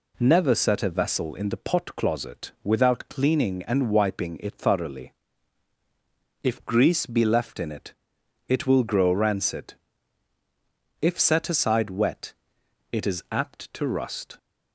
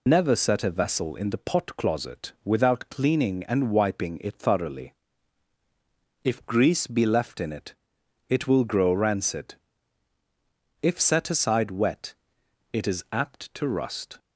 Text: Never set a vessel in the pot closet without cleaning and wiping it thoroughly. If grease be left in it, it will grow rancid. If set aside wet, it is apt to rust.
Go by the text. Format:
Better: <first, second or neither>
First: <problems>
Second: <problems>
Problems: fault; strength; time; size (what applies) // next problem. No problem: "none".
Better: first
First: none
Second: loses the start of "Never"; at 0.0 s; 110 ms